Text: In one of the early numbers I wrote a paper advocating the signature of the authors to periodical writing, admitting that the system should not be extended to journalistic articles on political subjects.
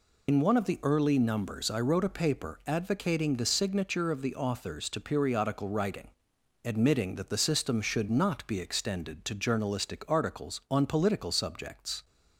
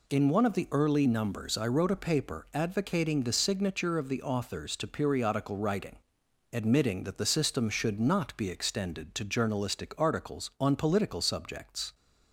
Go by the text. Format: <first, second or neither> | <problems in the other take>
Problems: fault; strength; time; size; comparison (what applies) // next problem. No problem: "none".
second | loses the start of "In"; at 0.2 s; 90 ms